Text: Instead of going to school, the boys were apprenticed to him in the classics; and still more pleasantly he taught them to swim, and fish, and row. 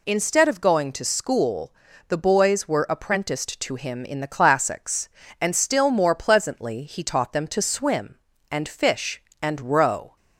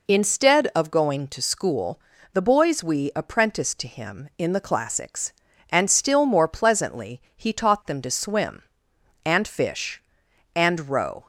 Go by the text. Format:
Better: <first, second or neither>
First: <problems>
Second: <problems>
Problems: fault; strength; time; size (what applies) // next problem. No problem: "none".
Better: first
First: none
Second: says "we" for "were"; at 2.8 s // pauses between "pleasantly" and "he"; slight; at 7.1 s; 0.16 s long